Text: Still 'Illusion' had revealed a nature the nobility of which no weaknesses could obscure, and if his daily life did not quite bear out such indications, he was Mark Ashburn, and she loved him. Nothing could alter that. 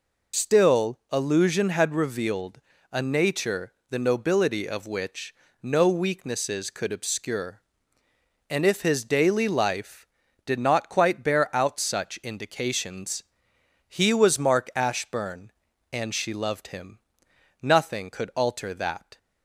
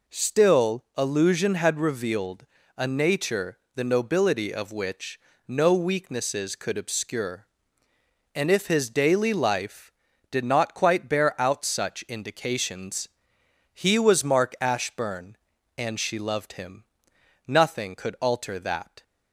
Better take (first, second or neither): second